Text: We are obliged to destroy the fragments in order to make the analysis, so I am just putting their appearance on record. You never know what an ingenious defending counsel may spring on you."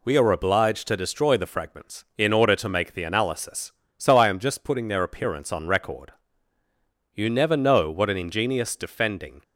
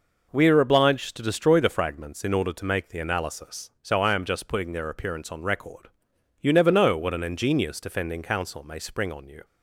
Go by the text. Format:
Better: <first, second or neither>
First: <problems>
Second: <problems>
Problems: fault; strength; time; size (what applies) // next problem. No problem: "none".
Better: second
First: stops before "counsel may spring on you"; at 9.4 s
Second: none